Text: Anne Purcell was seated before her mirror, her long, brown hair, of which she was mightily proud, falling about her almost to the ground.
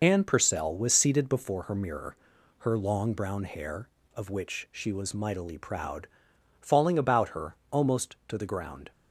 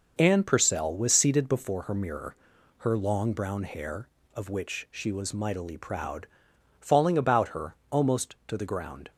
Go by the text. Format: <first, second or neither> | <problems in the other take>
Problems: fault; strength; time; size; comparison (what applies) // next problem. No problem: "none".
second | loses the start of "Anne"; at 0.0 s; 30 ms // pauses between "her" and "almost"; slight; at 7.5 s; 0.16 s long; slight in the second